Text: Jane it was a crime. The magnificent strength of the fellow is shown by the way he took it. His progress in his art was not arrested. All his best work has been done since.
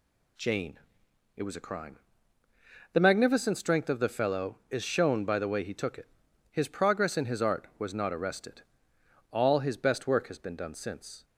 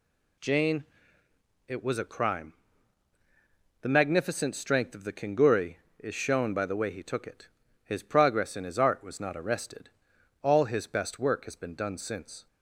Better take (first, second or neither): first